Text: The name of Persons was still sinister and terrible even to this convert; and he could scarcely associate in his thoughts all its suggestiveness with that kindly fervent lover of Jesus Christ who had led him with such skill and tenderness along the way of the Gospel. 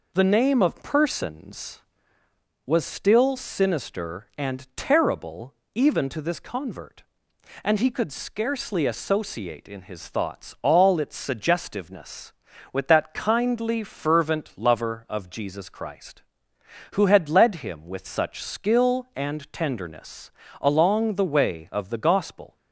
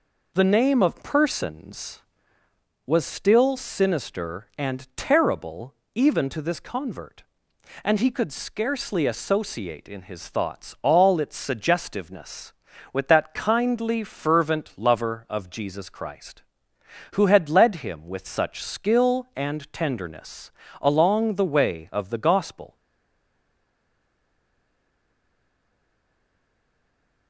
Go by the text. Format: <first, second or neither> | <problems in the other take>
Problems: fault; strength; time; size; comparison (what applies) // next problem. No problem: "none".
first | pauses between "terrible" and "even"; slight; at 5.7 s; 0.18 s long; slight in the first // pauses between "tenderness" and "along"; slight; at 20.5 s; 0.28 s long; slight in the first // stays silent after the last word; strong; from 22.7 s on; 4.5 s long